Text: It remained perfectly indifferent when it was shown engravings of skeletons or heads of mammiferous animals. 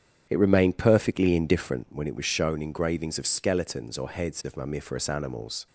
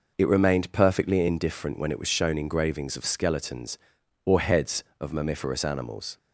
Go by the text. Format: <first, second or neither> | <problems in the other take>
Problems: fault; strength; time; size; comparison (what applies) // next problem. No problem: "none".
second | starts louder than the rest; strong; until 1.9 s; 8.5 dB